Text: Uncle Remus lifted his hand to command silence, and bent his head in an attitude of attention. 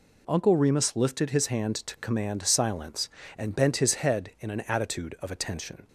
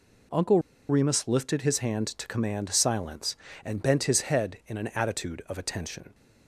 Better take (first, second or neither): first